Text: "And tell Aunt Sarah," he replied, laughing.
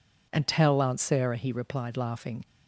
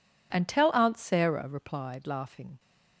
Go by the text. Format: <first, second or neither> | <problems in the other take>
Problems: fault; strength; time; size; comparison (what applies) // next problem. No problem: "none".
first | skips "he"; at 1.4 s